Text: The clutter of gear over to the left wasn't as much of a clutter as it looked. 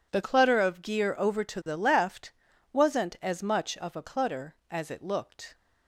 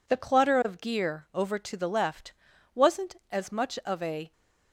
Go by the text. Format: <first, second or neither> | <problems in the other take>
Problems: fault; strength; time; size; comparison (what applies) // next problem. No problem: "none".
first | pauses between "left" and "wasn't"; at 2.3 s; 0.42 s long; also in the first // stops before "clutter as it looked"; at 4.3 s